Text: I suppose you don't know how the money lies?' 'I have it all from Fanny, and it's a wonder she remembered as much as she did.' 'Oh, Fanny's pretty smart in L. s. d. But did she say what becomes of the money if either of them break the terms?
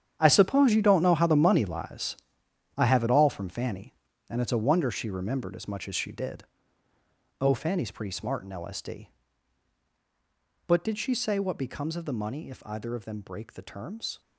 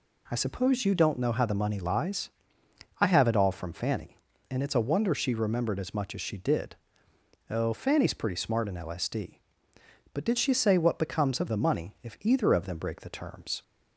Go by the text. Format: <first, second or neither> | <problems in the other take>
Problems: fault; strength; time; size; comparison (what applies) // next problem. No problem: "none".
second | gets quieter; strong; throughout; 13 dB